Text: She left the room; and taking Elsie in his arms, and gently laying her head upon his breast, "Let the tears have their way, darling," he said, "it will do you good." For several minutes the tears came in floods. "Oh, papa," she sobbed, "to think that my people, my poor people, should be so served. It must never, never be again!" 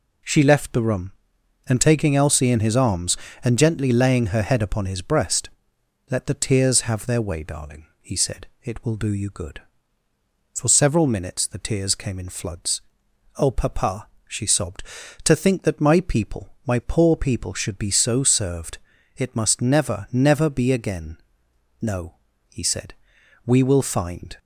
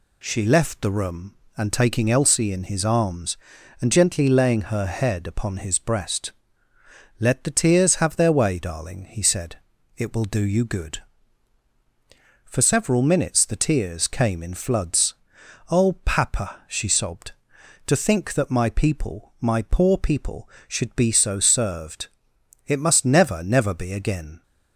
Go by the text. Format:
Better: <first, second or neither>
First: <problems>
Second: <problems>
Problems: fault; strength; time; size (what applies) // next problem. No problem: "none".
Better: second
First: goes on to say "No he said we will find"; strong; from 21.8 s on; 2.5 s long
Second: none